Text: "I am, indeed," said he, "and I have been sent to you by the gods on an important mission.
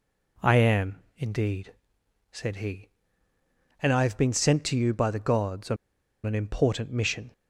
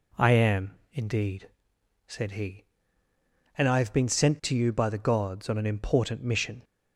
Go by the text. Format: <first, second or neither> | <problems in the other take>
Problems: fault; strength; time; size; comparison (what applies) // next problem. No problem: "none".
second | pauses between "on" and "an"; noticeable; at 5.7 s; 0.49 s long